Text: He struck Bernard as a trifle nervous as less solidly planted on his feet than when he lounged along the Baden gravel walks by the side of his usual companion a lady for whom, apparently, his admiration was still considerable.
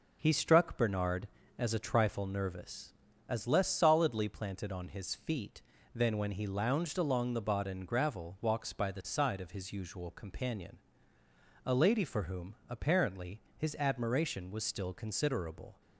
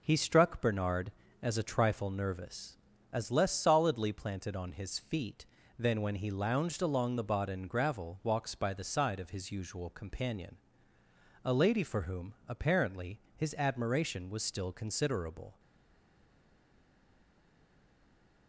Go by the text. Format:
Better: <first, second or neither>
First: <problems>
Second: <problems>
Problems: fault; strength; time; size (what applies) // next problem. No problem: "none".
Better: first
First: pauses between "companion" and "a"; noticeable; at 10.7 s; 0.90 s long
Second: pauses between "companion" and "a"; noticeable; at 10.5 s; 0.90 s long // stays silent after the last word; strong; from 15.5 s on; 2.9 s long